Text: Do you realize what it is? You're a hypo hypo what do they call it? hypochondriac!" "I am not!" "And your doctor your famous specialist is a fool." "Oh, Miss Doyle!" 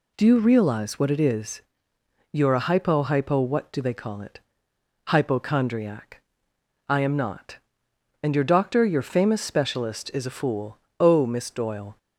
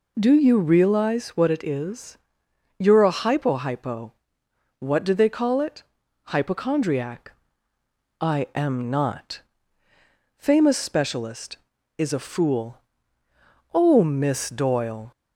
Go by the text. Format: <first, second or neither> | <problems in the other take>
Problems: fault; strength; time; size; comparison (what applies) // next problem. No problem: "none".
first | pauses between "hypo" and "what"; noticeable; at 4.1 s; 0.66 s long // skips "And your doctor your"; at 9.8 s